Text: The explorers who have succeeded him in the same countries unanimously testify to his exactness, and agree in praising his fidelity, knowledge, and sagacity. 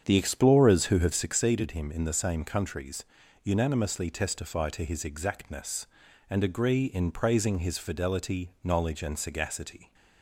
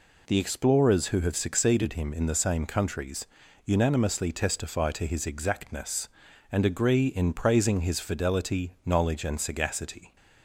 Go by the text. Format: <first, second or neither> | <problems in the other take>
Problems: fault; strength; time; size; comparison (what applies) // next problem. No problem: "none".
second | starts louder than the rest; strong; until 1.4 s; 7.5 dB // pauses between "countries" and "unanimously"; slight; at 3.0 s; 0.36 s long; slight in the second